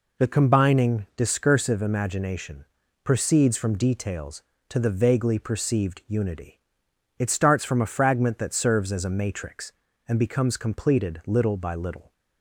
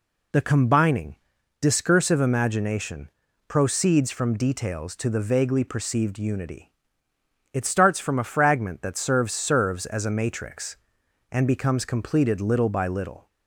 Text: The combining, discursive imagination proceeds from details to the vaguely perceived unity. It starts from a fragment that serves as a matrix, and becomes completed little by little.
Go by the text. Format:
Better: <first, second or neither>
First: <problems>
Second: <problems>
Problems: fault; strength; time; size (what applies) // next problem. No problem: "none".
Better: first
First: pauses between "imagination" and "proceeds"; at 2.6 s; 0.40 s long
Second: pauses between "imagination" and "proceeds"; at 3.0 s; 0.38 s long // says "serves" twice; at 9.3 s